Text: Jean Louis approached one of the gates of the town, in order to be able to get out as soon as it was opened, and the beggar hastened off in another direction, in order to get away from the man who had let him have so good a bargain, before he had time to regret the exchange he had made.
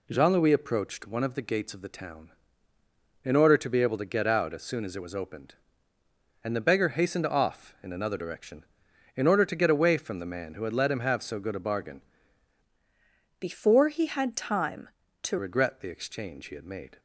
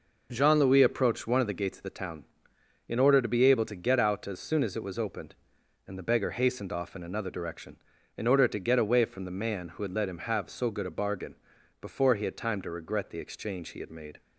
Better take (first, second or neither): second